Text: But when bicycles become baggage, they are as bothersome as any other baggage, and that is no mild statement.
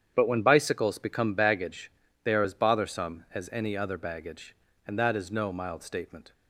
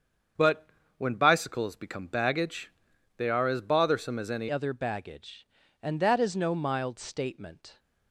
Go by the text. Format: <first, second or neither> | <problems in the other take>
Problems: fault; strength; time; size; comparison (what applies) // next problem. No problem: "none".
first | starts louder than the rest; strong; until 1.6 s; 7.5 dB; strong in the first // pauses between "But" and "when"; slight; at 0.6 s; 0.30 s long // changes voice at "other"; from 4.5 s on; 3.2 s long